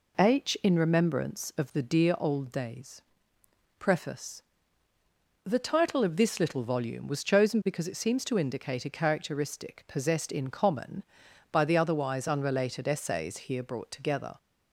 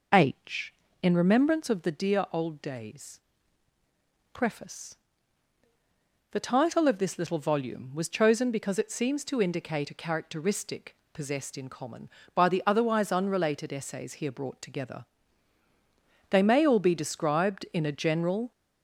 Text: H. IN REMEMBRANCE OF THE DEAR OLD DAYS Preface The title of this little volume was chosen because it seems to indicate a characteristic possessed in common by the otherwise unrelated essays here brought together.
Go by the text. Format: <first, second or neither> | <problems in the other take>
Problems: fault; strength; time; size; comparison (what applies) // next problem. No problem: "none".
first | pauses between "DAYS" and "Preface"; at 3.1 s; 1.1 s long; noticeable in the first // pauses between "Preface" and "The"; strong; at 4.9 s; 1.3 s long; also in the first // pauses between "characteristic" and "possessed"; slight; at 10.9 s; 0.18 s long // goes on to say "They may all be described in a general"; strong; from 16.2 s on; 2.2 s long